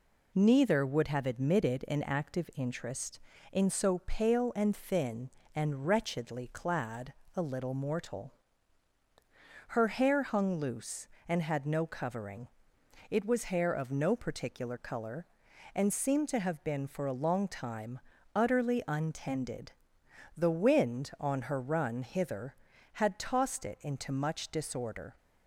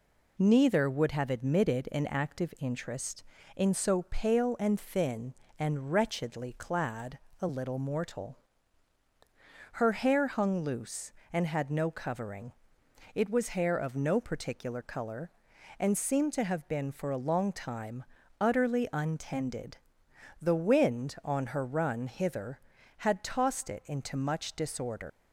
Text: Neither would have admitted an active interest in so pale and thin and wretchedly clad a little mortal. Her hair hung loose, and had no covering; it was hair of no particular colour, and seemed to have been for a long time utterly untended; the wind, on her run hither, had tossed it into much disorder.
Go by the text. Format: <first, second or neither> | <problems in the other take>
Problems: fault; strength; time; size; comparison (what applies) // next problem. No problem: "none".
first | pauses between "clad" and "a"; slight; at 7.1 s; 0.22 s long; slight in the first // pauses between "time" and "utterly"; slight; at 18.0 s; 0.36 s long; slight in the first // leaves "disorder" unfinished; at 25.0 s; 110 ms